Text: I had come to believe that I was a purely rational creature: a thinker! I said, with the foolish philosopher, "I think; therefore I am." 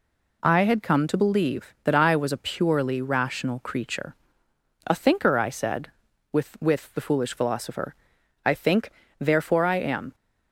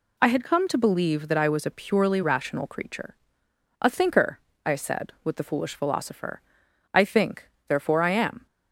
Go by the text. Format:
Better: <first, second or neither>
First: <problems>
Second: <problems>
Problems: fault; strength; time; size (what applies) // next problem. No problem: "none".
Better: second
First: says "with" twice; at 6.6 s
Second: none